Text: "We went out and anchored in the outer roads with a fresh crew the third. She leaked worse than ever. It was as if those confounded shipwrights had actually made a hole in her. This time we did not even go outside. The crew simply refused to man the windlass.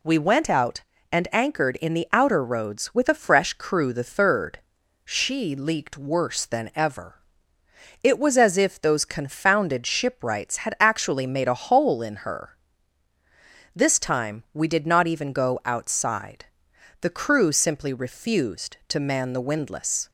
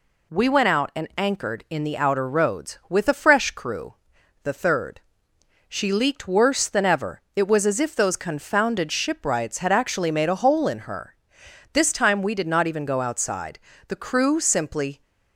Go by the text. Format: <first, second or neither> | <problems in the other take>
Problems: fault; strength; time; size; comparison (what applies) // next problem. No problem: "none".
first | pauses between "crew" and "the"; noticeable; at 3.9 s; 0.48 s long // stops before "refused to man the windlass"; at 15.0 s